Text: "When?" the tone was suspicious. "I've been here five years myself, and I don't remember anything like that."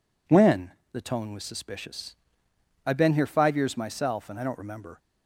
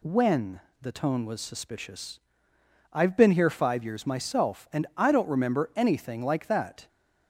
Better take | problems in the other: second | stops before "anything like that"; at 4.9 s

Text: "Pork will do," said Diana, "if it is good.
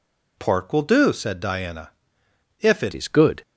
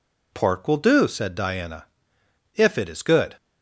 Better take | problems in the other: second | changes voice at "is"; from 2.9 s on; 0.5 s long

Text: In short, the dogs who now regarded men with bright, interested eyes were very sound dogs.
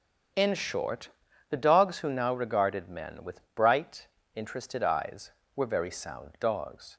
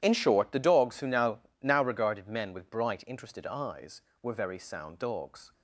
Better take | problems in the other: first | starts louder than the rest; strong; until 1.0 s; 11.5 dB; also in the first // says "now" twice; at 1.6 s

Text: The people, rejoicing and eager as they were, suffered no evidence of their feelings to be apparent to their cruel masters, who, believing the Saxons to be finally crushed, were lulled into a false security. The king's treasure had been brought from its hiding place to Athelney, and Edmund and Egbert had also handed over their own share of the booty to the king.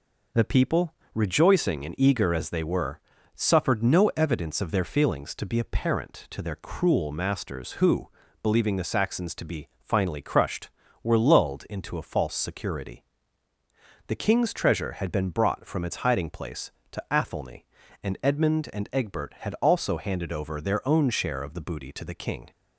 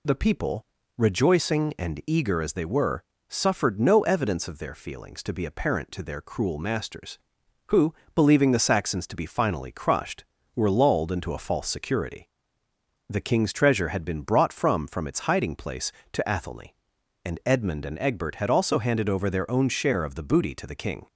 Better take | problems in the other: first | says "from" twice; at 14.8 s

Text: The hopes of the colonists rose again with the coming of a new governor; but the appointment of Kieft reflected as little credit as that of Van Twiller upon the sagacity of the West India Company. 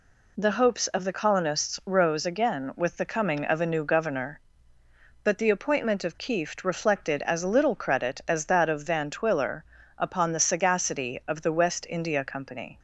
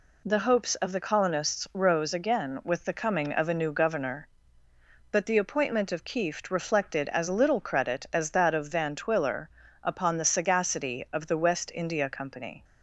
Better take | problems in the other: neither | pauses between "Twiller" and "upon"; slight; the same in both

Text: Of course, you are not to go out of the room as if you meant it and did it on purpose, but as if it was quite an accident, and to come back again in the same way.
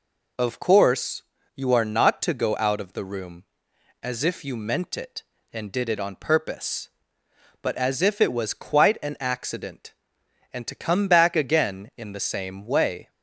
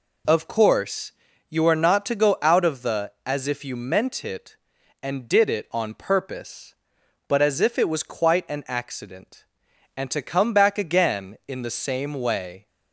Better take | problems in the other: first | skips "room"; at 3.1 s

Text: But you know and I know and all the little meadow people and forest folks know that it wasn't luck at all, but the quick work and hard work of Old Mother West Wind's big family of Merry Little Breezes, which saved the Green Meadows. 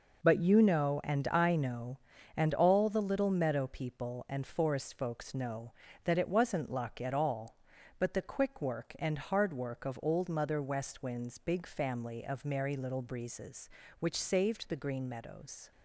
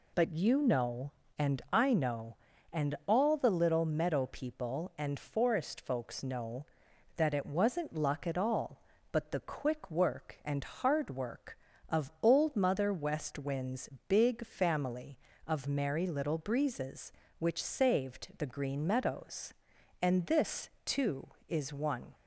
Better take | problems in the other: first | pauses between "Wind's" and "big"; slight; at 13.8 s; 0.20 s long // goes on to say "And this too is one"; strong; from 20.0 s on; 2.1 s long

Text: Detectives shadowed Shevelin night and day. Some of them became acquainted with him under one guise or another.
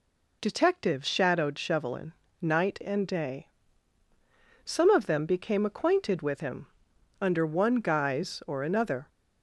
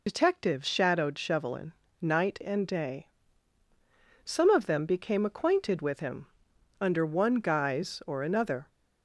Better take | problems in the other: first | loses the start of "Detectives"; at 0.0 s; 55 ms // pauses between "Shevelin" and "night"; slight; at 1.7 s; 0.28 s long; slight in the first // pauses between "him" and "under"; noticeable; at 6.2 s; 0.52 s long; noticeable in the first

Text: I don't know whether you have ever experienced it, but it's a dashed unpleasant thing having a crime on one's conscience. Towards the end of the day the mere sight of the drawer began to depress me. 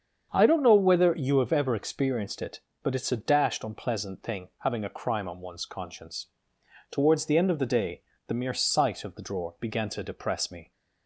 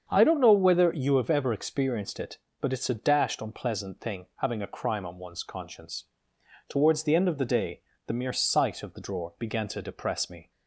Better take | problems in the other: neither | starts louder than the rest; strong; the same in both // pauses between "day" and "the"; slight; the same in both

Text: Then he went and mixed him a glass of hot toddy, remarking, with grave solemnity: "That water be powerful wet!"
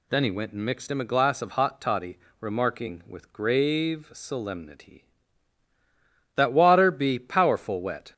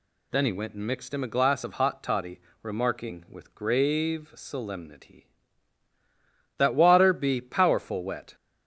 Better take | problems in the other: neither | none

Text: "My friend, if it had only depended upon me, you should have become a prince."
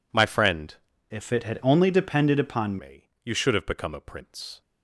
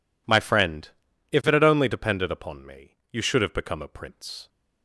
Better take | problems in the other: second | changes voice from "if" to "upon"; from 1.1 to 2.7 s; 1.6 s long

